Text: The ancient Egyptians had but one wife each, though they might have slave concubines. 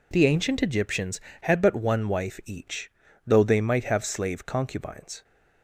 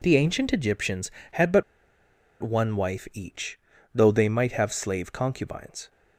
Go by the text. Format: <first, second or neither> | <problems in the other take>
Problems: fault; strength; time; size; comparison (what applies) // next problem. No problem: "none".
first | pauses between "but" and "one"; noticeable; at 1.6 s; 0.78 s long